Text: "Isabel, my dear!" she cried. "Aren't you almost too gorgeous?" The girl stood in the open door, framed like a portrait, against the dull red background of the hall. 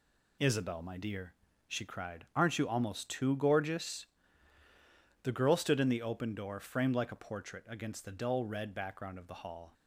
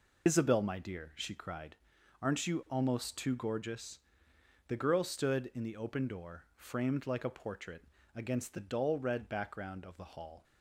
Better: first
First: none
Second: loses the start of "Isabel"; at 0.2 s; 75 ms

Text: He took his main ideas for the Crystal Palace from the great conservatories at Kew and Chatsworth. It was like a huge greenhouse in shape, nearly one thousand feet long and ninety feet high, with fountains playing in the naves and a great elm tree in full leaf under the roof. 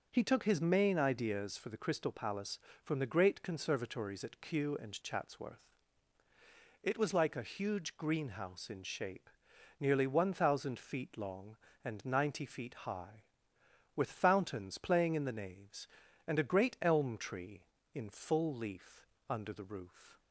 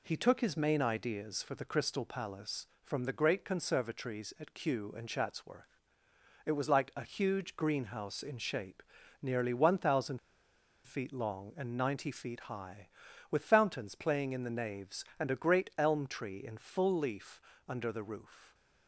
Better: first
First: pauses between "leaf" and "under"; slight; at 19.0 s; 0.24 s long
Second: pauses between "thousand" and "feet"; noticeable; at 10.1 s; 0.66 s long // pauses between "leaf" and "under"; slight; at 17.4 s; 0.26 s long

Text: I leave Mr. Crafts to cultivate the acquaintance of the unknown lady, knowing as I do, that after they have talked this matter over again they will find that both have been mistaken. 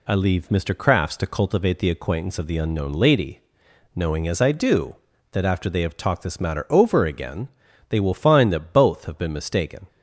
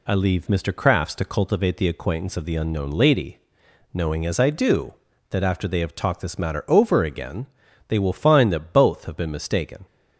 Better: neither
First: pauses between "again" and "they"; at 7.4 s; 0.41 s long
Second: pauses between "again" and "they"; at 7.4 s; 0.40 s long

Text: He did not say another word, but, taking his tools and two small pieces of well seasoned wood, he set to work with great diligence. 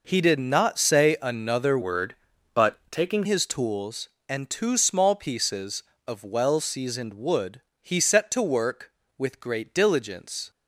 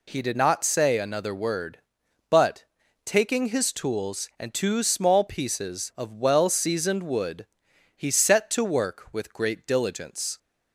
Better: second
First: changes voice from "word" to "taking"; from 1.8 to 3.2 s; 1.4 s long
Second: none

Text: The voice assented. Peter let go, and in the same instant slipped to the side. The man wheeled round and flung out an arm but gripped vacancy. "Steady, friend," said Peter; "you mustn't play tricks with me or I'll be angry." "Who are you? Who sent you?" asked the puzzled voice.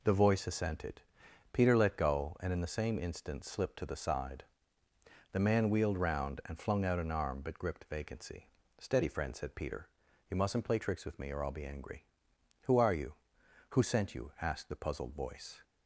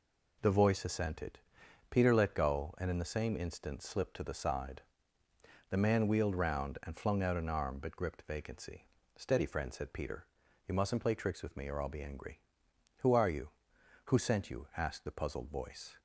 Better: neither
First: none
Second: none

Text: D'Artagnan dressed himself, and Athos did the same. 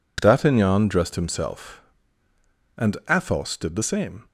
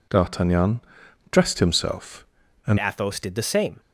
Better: first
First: none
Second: pauses between "D'Artagnan" and "dressed"; noticeable; at 0.8 s; 0.50 s long // changes voice at "Athos"; from 2.7 s on; 1.0 s long

